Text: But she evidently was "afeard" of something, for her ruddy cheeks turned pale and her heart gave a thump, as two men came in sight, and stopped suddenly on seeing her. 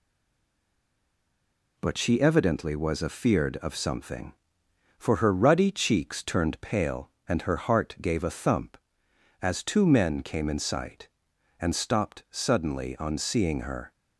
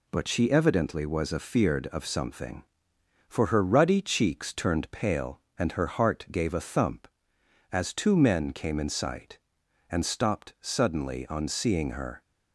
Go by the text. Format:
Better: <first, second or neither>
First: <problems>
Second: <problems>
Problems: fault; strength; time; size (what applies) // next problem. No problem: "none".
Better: second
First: stays silent before the first word; noticeable; until 1.7 s; 1.7 s long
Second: none